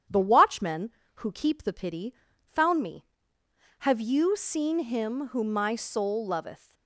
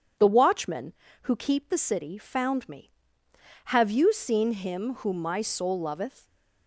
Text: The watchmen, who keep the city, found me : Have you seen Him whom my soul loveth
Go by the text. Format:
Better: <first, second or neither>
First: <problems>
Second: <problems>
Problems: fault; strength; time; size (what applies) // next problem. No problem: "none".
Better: second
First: starts louder than the rest; strong; until 1.3 s; 9 dB // says "pity" for "city"; at 1.7 s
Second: starts louder than the rest; strong; until 1.5 s; 8 dB